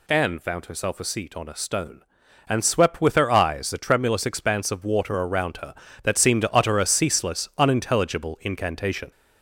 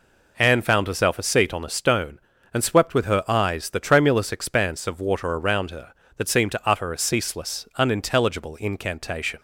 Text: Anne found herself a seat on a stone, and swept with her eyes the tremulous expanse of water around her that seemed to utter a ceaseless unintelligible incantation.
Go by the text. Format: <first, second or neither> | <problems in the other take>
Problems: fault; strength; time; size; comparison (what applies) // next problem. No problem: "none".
second | gets louder; noticeable; throughout; 4 dB